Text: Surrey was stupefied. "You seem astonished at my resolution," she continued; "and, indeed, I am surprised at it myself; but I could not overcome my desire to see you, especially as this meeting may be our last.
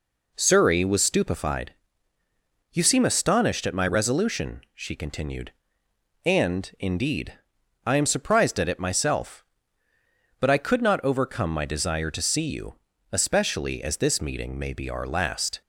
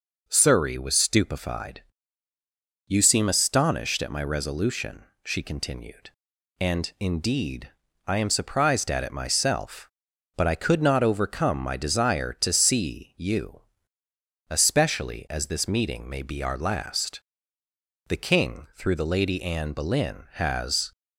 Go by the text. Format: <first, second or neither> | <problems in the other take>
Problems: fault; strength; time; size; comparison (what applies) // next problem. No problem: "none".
first | goes on to say "The king through the Lady Anne Boleyn has"; strong; from 18.0 s on; 2.8 s long